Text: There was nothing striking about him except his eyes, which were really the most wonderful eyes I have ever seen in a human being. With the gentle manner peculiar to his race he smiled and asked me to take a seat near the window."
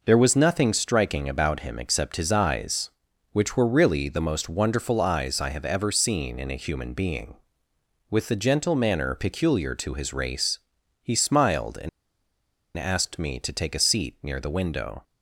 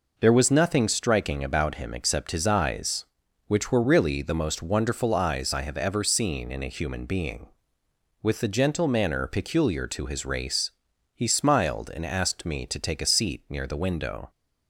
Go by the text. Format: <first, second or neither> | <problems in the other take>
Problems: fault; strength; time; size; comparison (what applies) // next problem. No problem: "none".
second | pauses between "race" and "he"; noticeable; at 10.5 s; 0.46 s long; noticeable in the second // pauses between "and" and "asked"; noticeable; at 11.8 s; 0.87 s long